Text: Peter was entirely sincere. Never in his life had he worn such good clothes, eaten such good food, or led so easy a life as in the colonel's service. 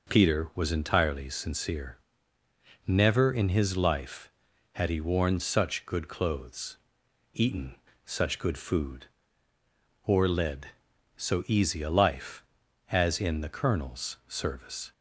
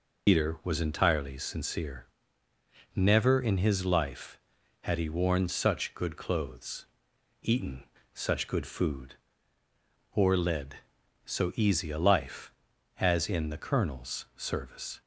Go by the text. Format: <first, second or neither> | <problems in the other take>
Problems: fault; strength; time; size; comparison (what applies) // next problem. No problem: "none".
first | loses the start of "Peter"; at 0.2 s; 115 ms // pauses between "eaten" and "such"; slight; at 7.8 s; 0.32 s long; slight in the first